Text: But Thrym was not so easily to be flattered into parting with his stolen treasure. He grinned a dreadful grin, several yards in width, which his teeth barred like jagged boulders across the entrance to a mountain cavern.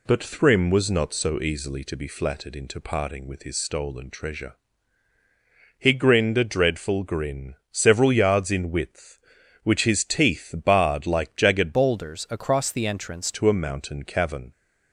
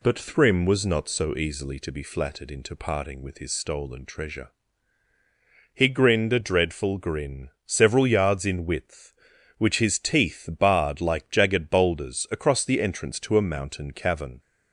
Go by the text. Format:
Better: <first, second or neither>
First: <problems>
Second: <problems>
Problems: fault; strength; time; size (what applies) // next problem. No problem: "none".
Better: second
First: changes voice from "boulders" to "entrance"; from 11.7 to 13.3 s; 1.6 s long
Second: none